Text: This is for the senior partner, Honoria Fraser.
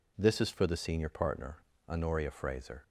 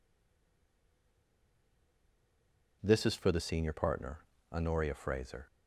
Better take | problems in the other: first | stays silent before the first word; strong; until 2.8 s; 2.8 s long

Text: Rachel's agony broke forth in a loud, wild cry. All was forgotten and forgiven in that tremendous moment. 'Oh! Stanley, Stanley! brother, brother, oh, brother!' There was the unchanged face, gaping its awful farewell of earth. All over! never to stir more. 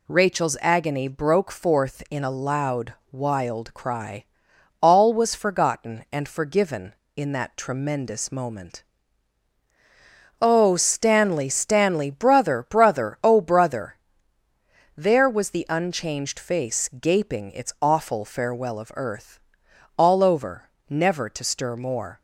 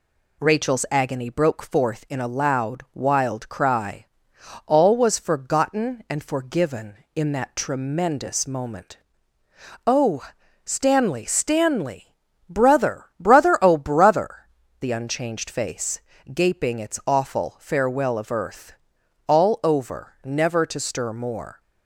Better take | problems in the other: first | skips "There was"; at 14.6 s

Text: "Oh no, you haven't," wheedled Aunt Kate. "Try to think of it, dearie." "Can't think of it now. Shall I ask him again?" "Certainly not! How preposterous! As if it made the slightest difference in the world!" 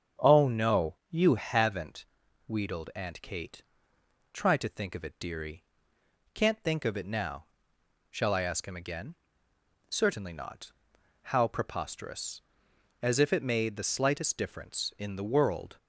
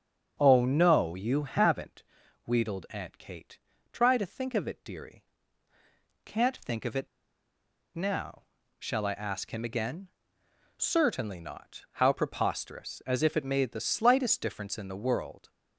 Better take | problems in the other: first | starts louder than the rest; strong; until 1.4 s; 7 dB; strong in the first // pauses between "it" and "now"; noticeable; at 7.0 s; 0.89 s long

